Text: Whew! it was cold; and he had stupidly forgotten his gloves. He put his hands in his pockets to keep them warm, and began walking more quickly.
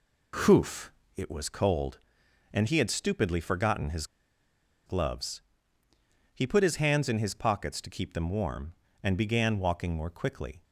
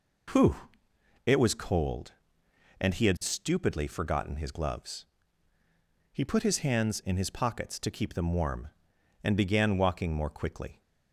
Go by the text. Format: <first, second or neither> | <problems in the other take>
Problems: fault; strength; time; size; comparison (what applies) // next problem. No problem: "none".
second | pauses between "his" and "gloves"; noticeable; at 4.0 s; 0.81 s long